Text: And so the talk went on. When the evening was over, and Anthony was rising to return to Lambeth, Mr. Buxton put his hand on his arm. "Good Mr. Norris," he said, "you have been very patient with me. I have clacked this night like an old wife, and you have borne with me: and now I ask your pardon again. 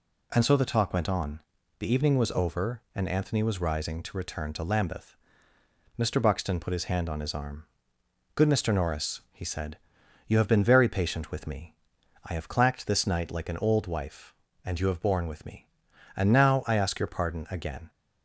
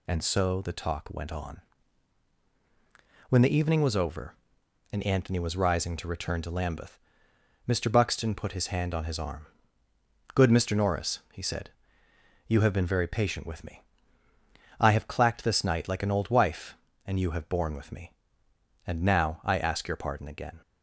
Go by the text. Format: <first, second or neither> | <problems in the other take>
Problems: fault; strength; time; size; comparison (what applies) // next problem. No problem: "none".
second | skips "When"; at 1.6 s